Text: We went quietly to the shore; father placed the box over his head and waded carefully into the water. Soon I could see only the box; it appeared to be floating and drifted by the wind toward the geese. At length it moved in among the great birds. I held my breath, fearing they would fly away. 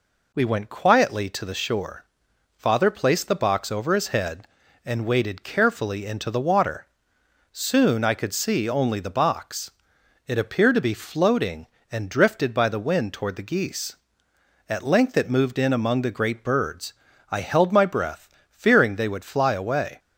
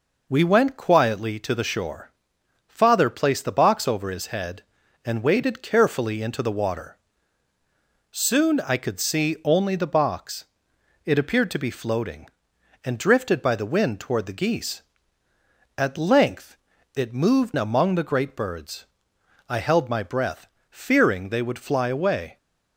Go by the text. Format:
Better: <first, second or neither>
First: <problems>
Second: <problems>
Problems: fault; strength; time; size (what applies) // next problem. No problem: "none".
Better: first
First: none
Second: pauses between "length" and "it"; slight; at 16.5 s; 0.36 s long // skips "in"; at 17.5 s